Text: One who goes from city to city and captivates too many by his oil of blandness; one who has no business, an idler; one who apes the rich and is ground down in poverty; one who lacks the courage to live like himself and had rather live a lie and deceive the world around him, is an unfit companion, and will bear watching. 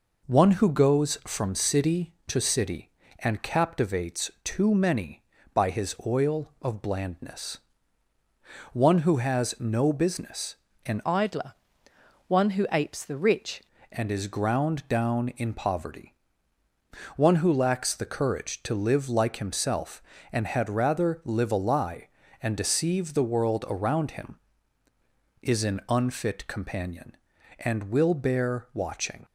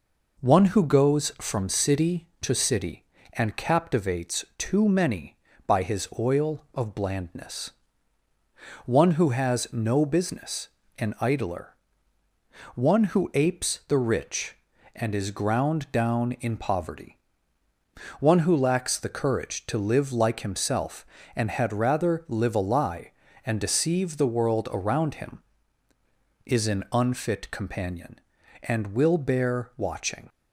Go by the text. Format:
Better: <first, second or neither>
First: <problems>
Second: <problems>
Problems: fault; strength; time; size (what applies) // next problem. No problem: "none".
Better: second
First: changes voice from "idler" to "rich"; from 11.0 to 13.6 s; 2.6 s long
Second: none